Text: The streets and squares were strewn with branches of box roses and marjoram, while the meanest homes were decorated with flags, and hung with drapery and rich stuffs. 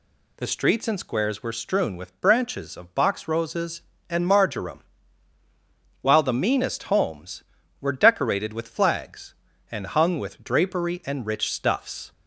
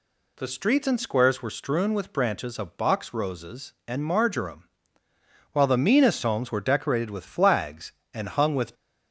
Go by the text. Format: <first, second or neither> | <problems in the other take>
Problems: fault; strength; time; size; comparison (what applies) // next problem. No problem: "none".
first | stops before "drapery and rich stuffs"; at 8.7 s